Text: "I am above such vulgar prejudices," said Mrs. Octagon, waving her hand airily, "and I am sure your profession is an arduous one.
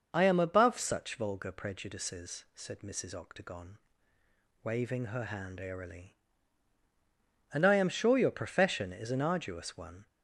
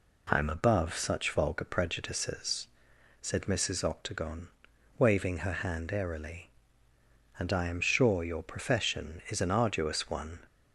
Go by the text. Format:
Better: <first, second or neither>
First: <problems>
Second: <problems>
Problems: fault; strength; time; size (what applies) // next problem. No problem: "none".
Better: neither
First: none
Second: none